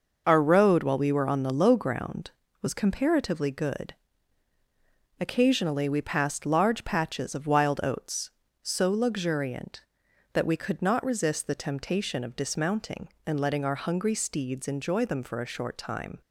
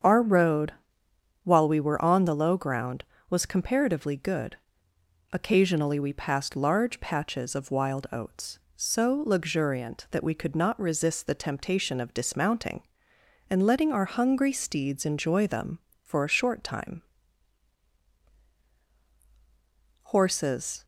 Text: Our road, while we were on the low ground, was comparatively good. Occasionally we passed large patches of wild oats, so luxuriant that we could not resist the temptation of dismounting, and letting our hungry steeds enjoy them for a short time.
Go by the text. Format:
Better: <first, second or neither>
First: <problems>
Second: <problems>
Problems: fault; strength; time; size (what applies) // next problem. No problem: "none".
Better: first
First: none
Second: starts louder than the rest; strong; until 1.7 s; 7.5 dB // goes on to say "Horses"; noticeable; from 20.0 s on; 0.82 s long